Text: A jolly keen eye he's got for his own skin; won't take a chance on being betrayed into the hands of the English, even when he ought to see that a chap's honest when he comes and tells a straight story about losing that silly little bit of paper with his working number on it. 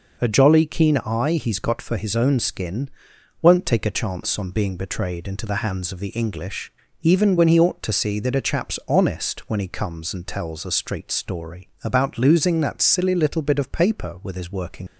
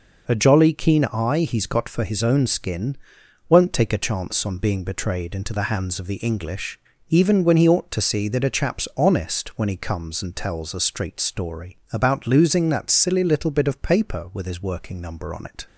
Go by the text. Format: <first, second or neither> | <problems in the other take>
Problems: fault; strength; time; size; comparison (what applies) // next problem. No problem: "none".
second | stops before "number on it"; at 14.8 s